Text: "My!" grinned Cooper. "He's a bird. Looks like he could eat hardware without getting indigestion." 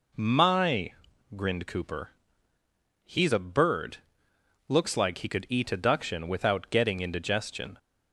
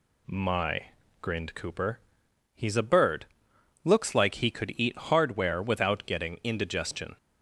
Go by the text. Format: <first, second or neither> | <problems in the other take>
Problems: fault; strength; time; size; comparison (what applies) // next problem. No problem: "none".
second | says "adduction" for "hardware"; at 5.6 s